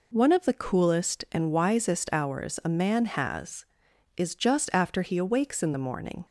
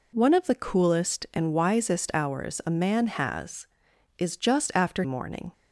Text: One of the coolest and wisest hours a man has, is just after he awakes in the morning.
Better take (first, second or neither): first